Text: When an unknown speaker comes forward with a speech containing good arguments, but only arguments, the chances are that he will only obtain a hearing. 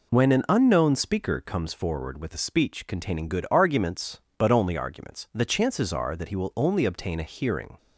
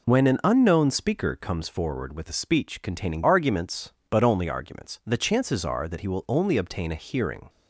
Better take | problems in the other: first | skips "good"; at 3.2 s

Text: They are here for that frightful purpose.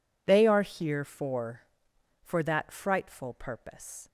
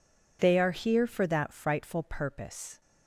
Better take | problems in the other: second | says "for" twice; at 2.2 s

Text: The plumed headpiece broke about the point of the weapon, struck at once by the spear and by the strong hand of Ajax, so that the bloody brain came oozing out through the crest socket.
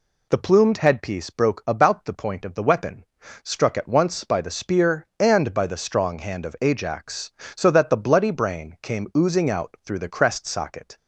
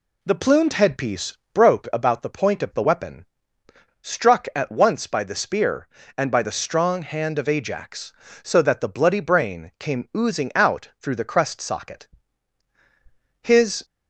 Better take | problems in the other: first | pauses between "headpiece" and "broke"; slight; at 1.3 s; 0.16 s long // goes on to say "His"; slight; from 13.4 s on; 0.42 s long

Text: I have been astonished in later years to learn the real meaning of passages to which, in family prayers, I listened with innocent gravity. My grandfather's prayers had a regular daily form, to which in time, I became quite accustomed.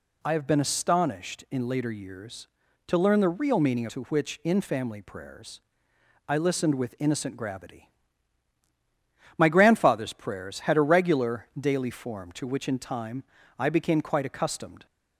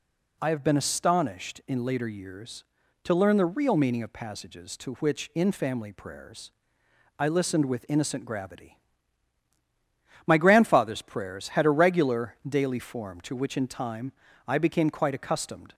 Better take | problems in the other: second | skips "of passages"; at 3.8 s

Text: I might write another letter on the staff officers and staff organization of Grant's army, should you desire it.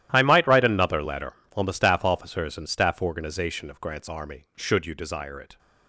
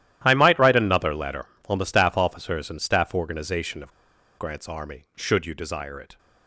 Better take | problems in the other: first | starts louder than the rest; strong; until 1.2 s; 13 dB; strong in the first // pauses between "of" and "Grant's"; at 3.9 s; 0.45 s long

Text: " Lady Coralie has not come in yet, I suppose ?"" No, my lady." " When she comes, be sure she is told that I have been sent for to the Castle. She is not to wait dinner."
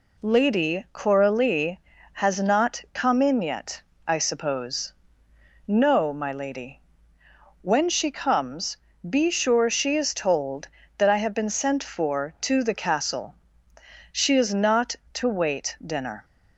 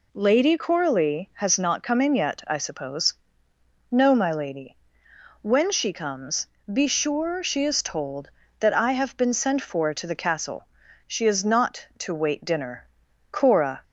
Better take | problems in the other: first | goes on to say "Cora"; from 13.3 s on; 0.52 s long

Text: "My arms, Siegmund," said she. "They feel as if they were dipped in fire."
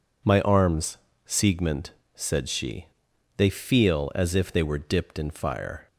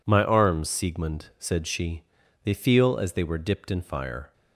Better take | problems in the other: first | skips "if"; at 3.1 s

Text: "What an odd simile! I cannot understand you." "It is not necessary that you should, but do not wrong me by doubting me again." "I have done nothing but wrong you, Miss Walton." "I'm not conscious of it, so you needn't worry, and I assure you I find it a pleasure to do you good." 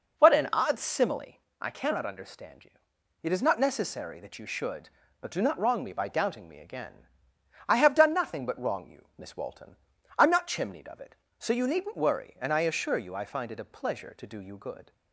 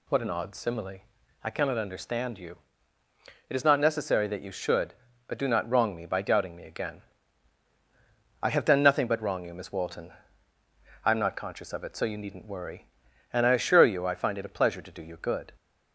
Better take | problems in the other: second | says "chimneyed" for "conscious"; at 10.4 s

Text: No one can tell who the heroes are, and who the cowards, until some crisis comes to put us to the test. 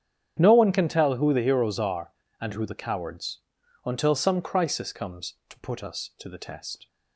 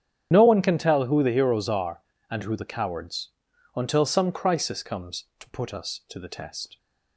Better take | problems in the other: first | loses the start of "No"; at 0.3 s; 35 ms // starts louder than the rest; strong; until 1.3 s; 9 dB; strong in the first

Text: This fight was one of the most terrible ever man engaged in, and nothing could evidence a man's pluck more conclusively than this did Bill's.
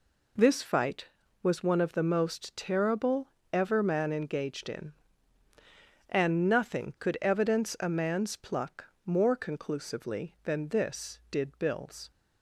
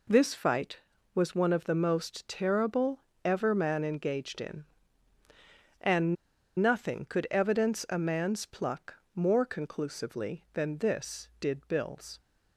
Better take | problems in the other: first | pauses between "terrible" and "ever"; slight; at 3.0 s; 0.26 s long; slight in the first // pauses between "and" and "nothing"; at 6.1 s; 0.44 s long // pauses between "pluck" and "more"; slight; at 8.9 s; 0.18 s long; slight in the first

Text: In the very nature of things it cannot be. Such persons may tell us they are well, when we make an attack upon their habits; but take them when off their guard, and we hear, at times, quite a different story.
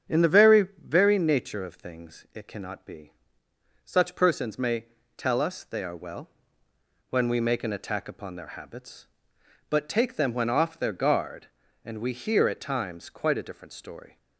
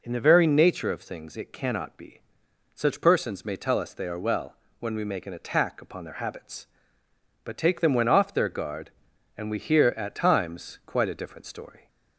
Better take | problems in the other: second | starts louder than the rest; strong; until 1.2 s; 8 dB // says "very" twice; at 0.8 s // pauses between "may" and "tell"; slight; at 4.8 s; 0.32 s long

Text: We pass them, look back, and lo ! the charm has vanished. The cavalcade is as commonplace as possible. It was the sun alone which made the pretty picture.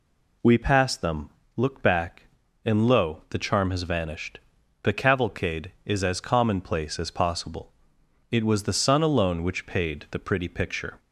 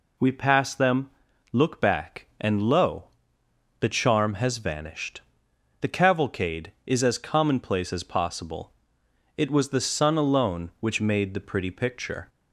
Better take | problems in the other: second | says "paid" for "made"; at 9.6 s

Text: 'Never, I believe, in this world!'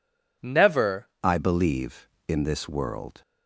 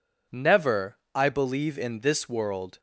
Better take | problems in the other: second | changes voice at "I"; from 1.2 s on; 2.0 s long

